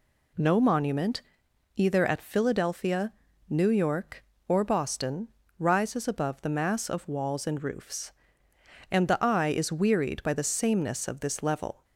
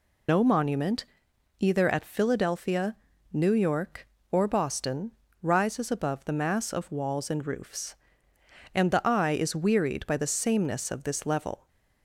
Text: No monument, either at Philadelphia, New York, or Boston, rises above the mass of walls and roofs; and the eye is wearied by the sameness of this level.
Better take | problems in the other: first | loses the start of "No"; at 0.2 s; 100 ms

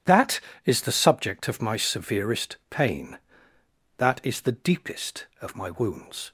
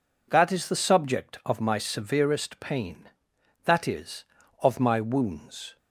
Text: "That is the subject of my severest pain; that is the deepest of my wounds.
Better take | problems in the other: first | skips "the deepest"; at 4.4 s

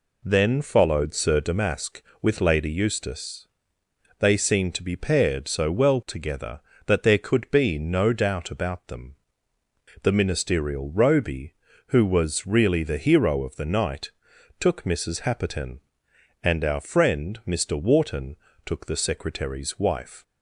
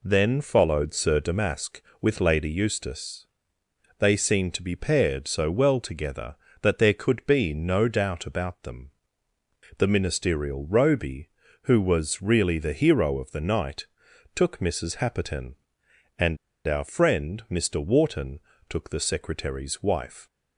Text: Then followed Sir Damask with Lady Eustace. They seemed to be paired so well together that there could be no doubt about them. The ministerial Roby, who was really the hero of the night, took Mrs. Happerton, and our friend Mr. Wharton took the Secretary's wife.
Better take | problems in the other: first | pauses between "and" and "our"; slight; at 16.3 s; 0.31 s long // pauses between "Wharton" and "took"; slight; at 18.4 s; 0.28 s long; slight in the first

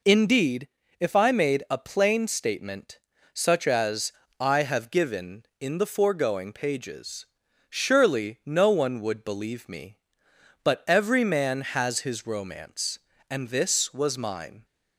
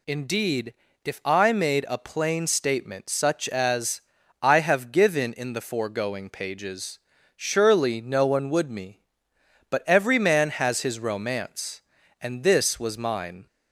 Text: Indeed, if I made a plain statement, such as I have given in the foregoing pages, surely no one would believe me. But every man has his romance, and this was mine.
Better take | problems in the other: first | pauses between "as" and "I"; at 3.9 s; 0.42 s long; slight in the first // skips "believe"; at 8.6 s

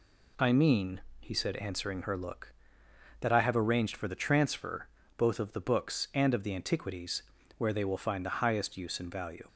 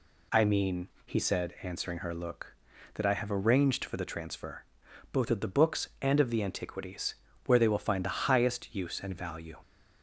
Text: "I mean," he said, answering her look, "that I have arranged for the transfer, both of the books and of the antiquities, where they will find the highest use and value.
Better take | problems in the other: neither | none

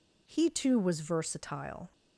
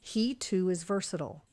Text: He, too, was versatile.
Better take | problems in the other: first | says "is" for "was"; at 0.6 s

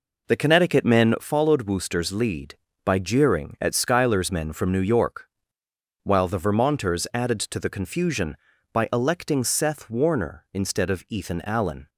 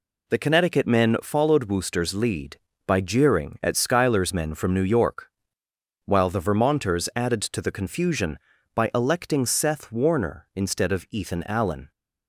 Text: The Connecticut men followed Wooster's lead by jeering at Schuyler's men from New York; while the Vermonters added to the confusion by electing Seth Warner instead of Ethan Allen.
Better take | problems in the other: second | starts louder than the rest; noticeable; until 1.2 s; 4.5 dB

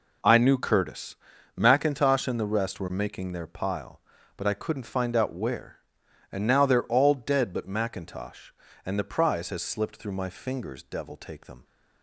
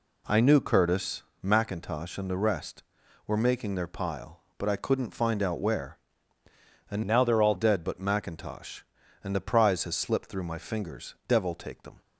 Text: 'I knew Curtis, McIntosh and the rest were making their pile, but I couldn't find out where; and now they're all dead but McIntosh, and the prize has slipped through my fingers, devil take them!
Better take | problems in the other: first | changes voice from "now" to "all"; from 7.0 to 7.5 s; 0.5 s long

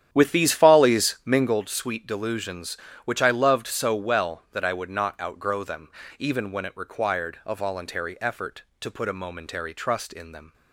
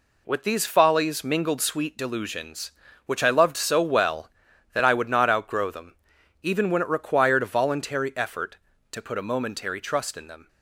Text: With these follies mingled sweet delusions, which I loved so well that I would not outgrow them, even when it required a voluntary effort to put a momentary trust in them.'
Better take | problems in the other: second | starts louder than the rest; strong; until 1.6 s; 10 dB

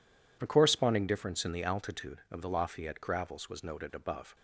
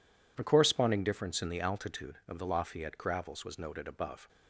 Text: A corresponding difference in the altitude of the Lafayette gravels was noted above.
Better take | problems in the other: neither | none

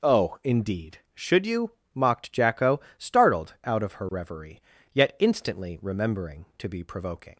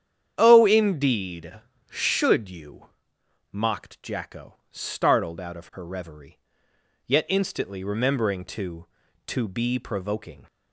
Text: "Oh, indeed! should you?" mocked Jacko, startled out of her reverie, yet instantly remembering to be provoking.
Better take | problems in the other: first | starts louder than the rest; strong; until 1.3 s; 9 dB // says "to" twice; at 9.2 s

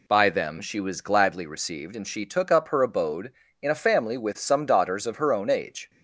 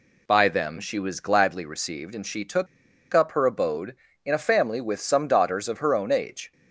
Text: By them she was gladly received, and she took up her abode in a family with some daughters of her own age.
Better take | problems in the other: first | pauses between "took" and "up"; noticeable; at 2.6 s; 0.47 s long

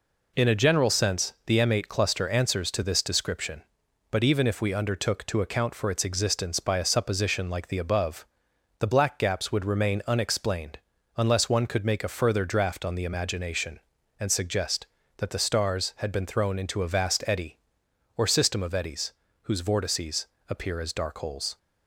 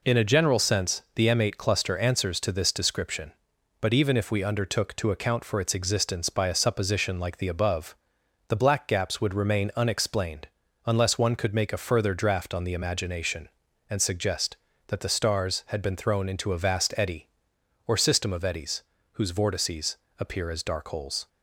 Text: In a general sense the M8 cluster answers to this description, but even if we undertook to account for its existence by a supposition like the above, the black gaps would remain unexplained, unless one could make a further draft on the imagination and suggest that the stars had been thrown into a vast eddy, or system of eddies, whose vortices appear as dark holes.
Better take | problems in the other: neither | pauses between "vortices" and "appear"; slight; the same in both

